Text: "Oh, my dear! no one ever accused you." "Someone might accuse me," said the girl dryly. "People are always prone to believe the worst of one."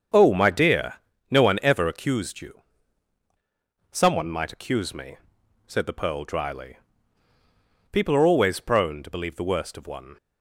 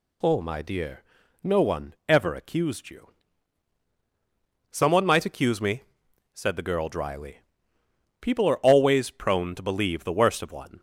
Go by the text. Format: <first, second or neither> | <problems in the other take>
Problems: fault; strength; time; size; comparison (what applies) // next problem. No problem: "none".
second | starts louder than the rest; strong; until 1.4 s; 7.5 dB // says "pearl" for "girl"; at 5.9 s